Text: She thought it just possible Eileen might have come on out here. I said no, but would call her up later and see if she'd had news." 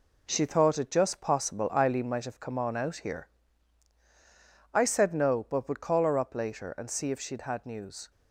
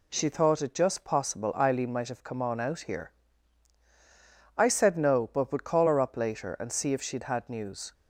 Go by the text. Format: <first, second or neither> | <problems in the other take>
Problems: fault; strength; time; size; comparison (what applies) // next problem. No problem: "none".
second | gets quieter; throughout; 6.5 dB